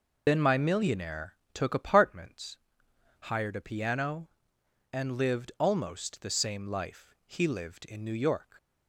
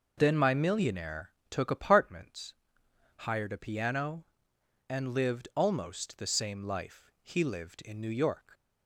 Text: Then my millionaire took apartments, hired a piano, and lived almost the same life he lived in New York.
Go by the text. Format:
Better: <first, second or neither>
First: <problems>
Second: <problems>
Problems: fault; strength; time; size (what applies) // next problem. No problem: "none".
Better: second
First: loses the start of "Then"; at 0.2 s; 60 ms // pauses between "millionaire" and "took"; slight; at 1.3 s; 0.18 s long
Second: pauses between "millionaire" and "took"; slight; at 1.3 s; 0.18 s long